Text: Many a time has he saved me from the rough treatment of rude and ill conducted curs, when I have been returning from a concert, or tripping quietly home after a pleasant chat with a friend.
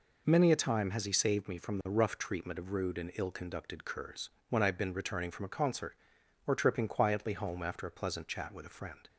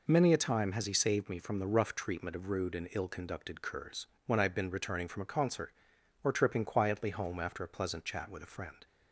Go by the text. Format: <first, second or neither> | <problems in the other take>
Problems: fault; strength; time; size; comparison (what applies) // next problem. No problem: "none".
neither | none